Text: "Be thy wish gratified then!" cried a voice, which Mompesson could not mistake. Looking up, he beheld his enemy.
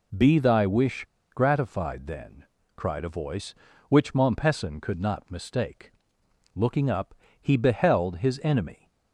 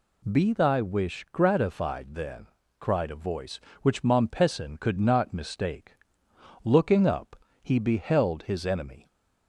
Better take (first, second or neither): second